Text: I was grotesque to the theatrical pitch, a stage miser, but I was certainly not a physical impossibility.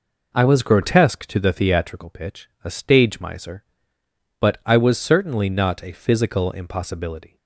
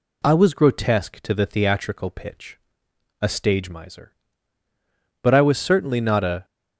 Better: first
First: none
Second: stops before "physical impossibility"; at 6.4 s

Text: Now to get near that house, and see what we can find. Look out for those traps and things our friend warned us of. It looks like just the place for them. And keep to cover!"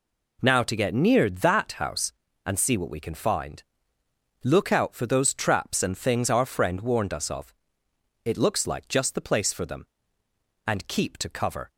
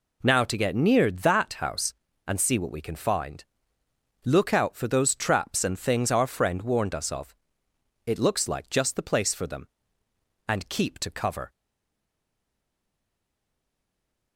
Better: first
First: none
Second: stays silent after the last word; strong; from 11.5 s on; 2.8 s long

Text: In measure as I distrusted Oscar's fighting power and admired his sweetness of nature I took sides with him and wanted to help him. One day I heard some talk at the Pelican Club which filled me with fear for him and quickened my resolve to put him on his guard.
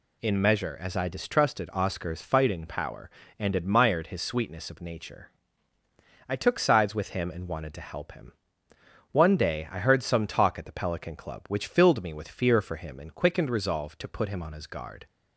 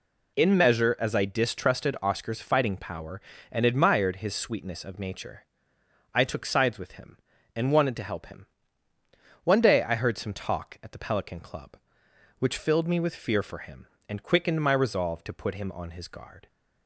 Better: second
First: pauses between "nature" and "I"; noticeable; at 5.2 s; 0.98 s long // skips "my"; at 13.4 s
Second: pauses between "nature" and "I"; noticeable; at 5.4 s; 0.68 s long

